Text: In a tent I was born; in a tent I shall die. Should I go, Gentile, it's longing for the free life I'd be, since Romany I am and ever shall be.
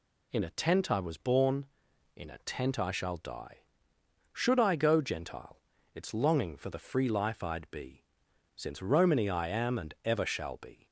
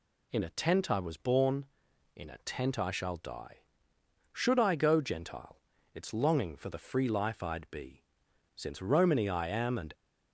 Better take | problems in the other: first | stops before "ever shall be"; at 9.9 s

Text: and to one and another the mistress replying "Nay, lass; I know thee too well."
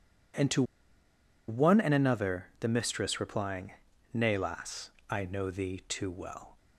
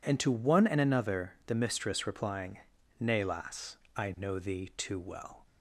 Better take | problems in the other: second | pauses between "to" and "one"; noticeable; at 0.6 s; 0.85 s long // pauses between "replying" and "Nay"; at 3.7 s; 0.42 s long; also in the second

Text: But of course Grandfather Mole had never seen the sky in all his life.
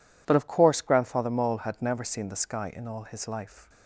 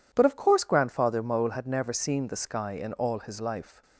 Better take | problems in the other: neither | none

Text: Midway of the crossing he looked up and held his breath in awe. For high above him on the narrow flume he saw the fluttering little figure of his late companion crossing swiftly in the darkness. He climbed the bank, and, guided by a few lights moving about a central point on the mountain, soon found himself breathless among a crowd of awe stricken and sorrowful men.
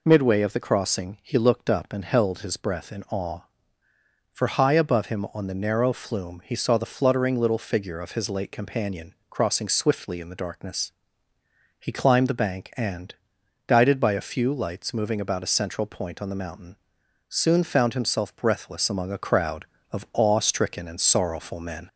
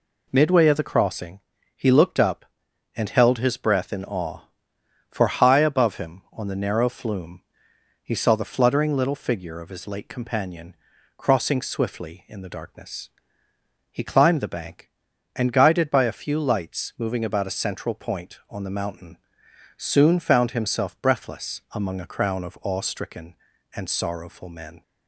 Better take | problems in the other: first | pauses between "crossing" and "he"; slight; at 1.3 s; 0.34 s long // pauses between "flume" and "he"; noticeable; at 7.4 s; 0.62 s long // pauses between "companion" and "crossing"; at 10.7 s; 0.40 s long; slight in the first // says "crown" for "crowd"; at 22.0 s

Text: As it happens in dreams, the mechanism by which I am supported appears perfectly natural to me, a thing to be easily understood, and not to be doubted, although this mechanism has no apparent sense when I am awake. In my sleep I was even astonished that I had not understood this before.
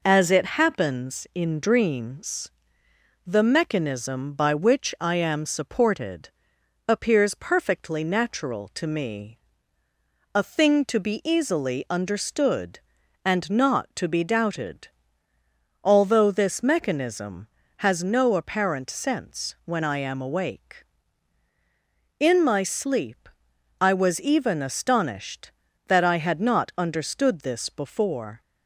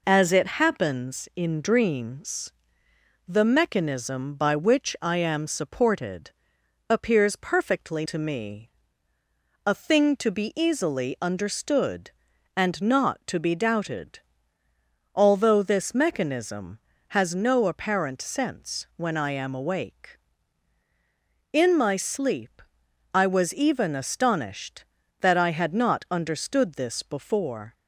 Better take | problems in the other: first | pauses between "supported" and "appears"; noticeable; at 6.3 s; 0.58 s long; noticeable in the first // skips "natural"; at 8.0 s // pauses between "sleep" and "I"; noticeable; at 22.6 s; 0.54 s long; noticeable in the first

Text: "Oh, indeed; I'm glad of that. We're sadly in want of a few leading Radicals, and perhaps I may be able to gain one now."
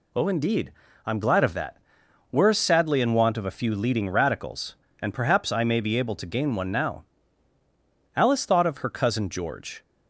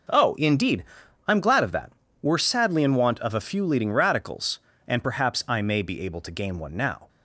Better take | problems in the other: second | goes on to say "Alice thought of her cousin George"; strong; from 8.1 s on; 1.6 s long

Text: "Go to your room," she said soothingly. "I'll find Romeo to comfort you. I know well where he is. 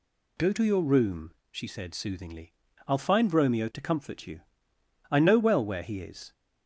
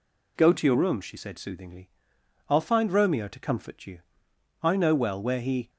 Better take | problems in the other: first | stops before "is"; at 5.6 s

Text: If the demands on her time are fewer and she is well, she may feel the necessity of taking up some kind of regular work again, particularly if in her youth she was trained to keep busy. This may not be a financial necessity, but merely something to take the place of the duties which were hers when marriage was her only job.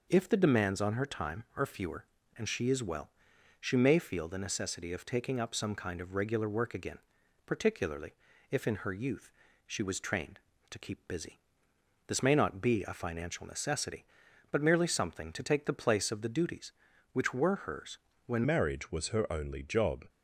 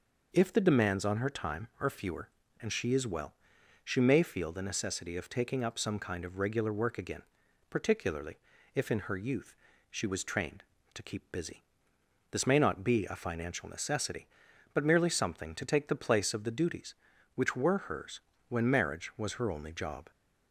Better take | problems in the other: second | pauses between "particularly" and "if"; slight; at 8.1 s; 0.36 s long; slight in the second // pauses between "youth" and "she"; slight; at 9.2 s; 0.36 s long; slight in the second // pauses between "hers" and "when"; slight; at 17.9 s; 0.28 s long; slight in the second // changes voice at "marriage"; from 18.4 s on; 1.6 s long

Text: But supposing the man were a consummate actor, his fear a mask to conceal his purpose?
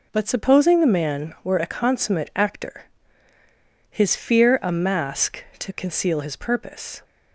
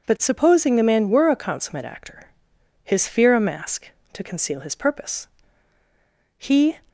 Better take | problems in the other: first | goes on to say "He"; slight; from 6.3 s on; 0.40 s long

